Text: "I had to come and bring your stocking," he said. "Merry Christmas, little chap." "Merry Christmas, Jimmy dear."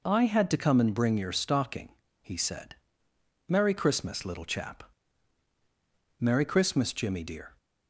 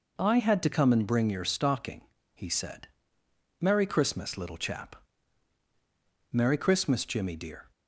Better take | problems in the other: neither | none

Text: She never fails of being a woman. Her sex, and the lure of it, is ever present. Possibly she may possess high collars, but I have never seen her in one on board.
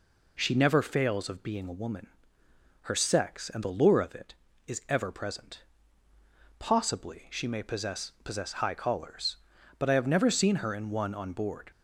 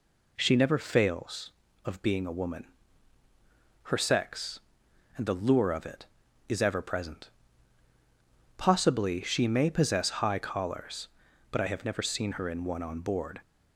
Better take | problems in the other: second | says "possess" twice; at 8.2 s

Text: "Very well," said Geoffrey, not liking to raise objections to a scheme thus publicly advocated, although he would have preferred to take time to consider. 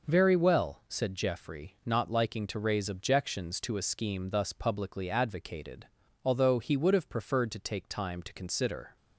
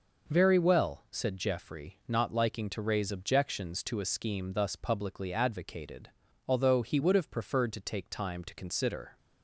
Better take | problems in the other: neither | none

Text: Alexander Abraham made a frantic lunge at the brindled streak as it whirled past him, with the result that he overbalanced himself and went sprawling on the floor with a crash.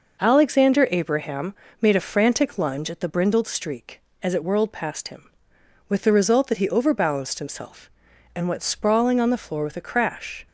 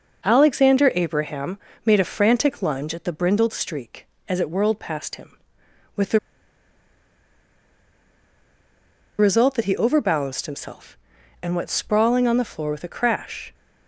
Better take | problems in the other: first | pauses between "Abraham" and "made"; slight; at 1.5 s; 0.26 s long; slight in the first // pauses between "the" and "result"; strong; at 6.1 s; 3.0 s long

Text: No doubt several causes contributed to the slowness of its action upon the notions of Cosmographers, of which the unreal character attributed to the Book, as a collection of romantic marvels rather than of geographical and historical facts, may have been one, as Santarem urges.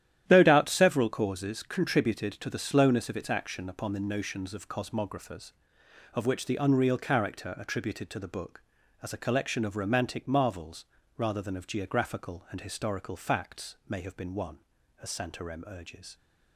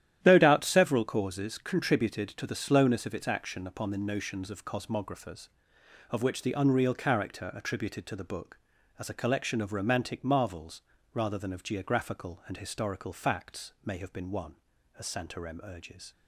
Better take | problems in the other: neither | starts louder than the rest; strong; the same in both // pauses between "marvels" and "rather"; slight; the same in both

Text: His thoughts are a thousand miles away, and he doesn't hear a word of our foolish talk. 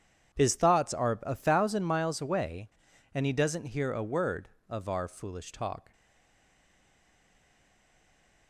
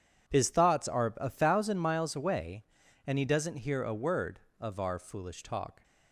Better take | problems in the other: second | stays silent after the last word; strong; from 5.9 s on; 2.5 s long

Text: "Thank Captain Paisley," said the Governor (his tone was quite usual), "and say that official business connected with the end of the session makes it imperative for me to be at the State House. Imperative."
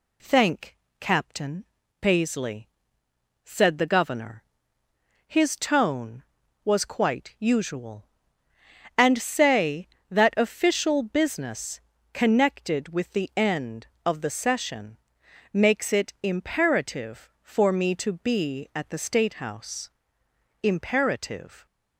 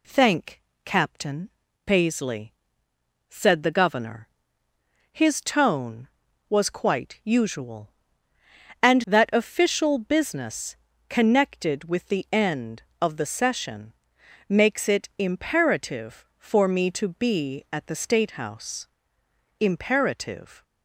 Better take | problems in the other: first | pauses between "Thank" and "Captain"; slight; at 0.6 s; 0.22 s long; slight in the first // pauses between "Captain" and "Paisley"; slight; at 1.4 s; 0.34 s long; slight in the first // skips "say"; at 9.0 s // pauses between "business" and "connected"; slight; at 10.7 s; 0.32 s long; slight in the first // pauses between "session" and "makes"; noticeable; at 13.9 s; 0.54 s long; noticeable in the first

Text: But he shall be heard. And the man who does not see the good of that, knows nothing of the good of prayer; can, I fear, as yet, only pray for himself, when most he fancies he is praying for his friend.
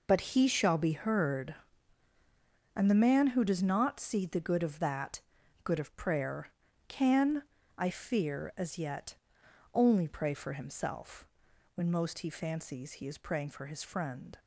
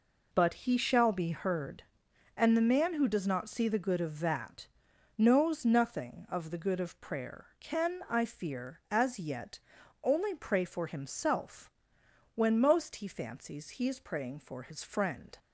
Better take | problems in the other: second | skips "knows nothing of the"; at 5.4 s

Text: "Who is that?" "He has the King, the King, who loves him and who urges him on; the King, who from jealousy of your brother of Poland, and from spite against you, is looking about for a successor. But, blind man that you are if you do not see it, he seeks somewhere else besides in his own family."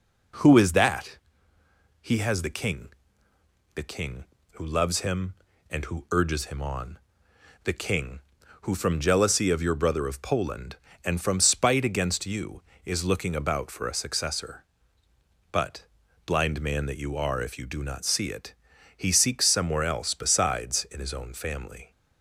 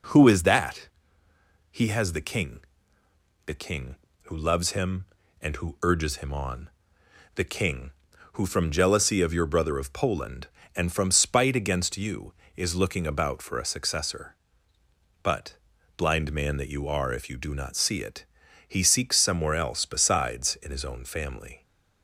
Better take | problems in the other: neither | none

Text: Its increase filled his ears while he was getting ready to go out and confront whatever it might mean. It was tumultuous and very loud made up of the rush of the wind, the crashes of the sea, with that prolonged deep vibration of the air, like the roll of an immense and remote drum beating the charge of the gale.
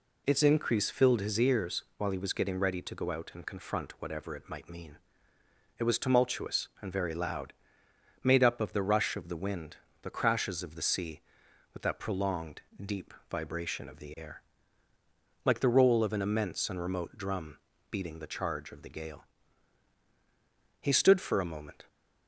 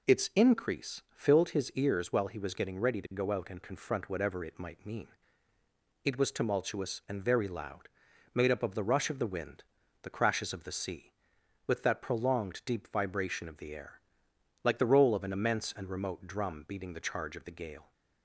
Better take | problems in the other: second | pauses between "ears" and "while"; slight; at 1.8 s; 0.16 s long // pauses between "loud" and "made"; noticeable; at 7.5 s; 0.74 s long; noticeable in the second // pauses between "prolonged" and "deep"; slight; at 12.6 s; 0.20 s long // pauses between "deep" and "vibration"; slight; at 13.1 s; 0.18 s long // pauses between "drum" and "beating"; slight; at 17.5 s; 0.32 s long // goes on to say "He stood for a moment"; noticeable; from 20.8 s on; 1.0 s long

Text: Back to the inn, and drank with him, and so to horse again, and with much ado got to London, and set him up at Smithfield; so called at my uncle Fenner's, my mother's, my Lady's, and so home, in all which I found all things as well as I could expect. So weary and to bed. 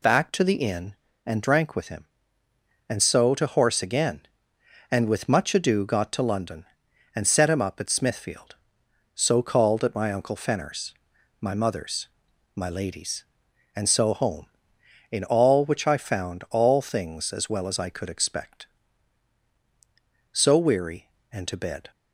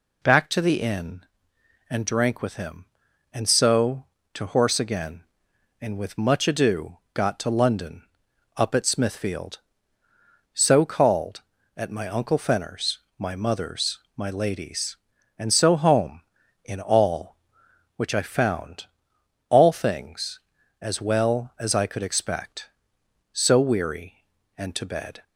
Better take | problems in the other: first | skips "and set him"; at 8.2 s // pauses between "found" and "all"; noticeable; at 18.8 s; 0.62 s long

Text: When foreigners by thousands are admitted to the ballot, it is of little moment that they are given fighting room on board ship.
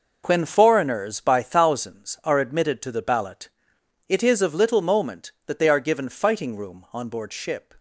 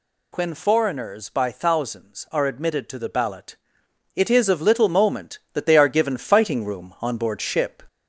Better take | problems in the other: first | gets louder; slight; throughout; 2 dB

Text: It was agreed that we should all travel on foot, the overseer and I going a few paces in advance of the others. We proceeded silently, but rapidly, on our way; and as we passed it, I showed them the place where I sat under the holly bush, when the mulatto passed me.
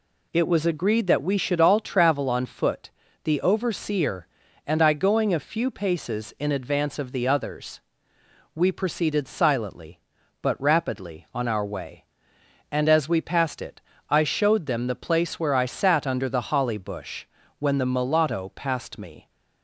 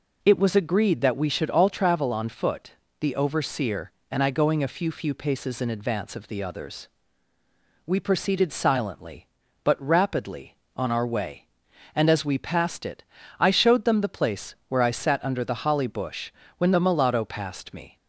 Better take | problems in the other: first | says "few" twice; at 4.9 s

